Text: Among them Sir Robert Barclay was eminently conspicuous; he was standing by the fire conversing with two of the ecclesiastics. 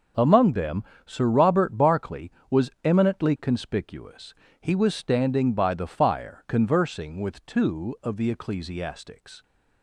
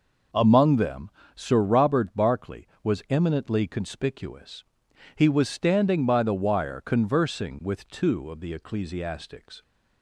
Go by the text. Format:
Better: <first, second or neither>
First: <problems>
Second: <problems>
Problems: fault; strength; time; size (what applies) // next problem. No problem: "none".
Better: first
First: pauses between "them" and "Sir"; slight; at 0.8 s; 0.22 s long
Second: pauses between "them" and "Sir"; slight; at 1.0 s; 0.26 s long // says "wire" for "fire"; at 6.3 s